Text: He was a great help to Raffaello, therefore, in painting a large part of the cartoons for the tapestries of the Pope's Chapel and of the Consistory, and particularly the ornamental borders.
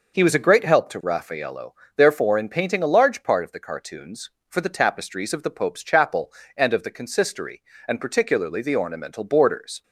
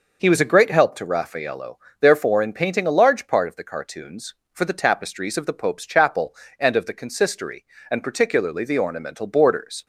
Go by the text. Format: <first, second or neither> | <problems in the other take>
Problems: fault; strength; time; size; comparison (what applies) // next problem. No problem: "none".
neither | none